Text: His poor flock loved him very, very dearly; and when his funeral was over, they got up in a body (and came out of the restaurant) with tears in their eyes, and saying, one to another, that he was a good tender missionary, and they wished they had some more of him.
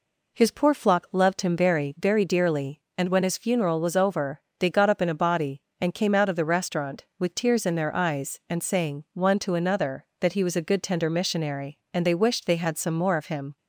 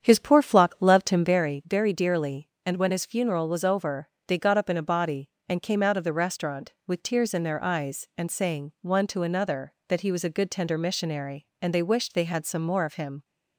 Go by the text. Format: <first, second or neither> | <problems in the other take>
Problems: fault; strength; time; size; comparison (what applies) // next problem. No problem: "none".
first | starts louder than the rest; strong; until 1.4 s; 8.5 dB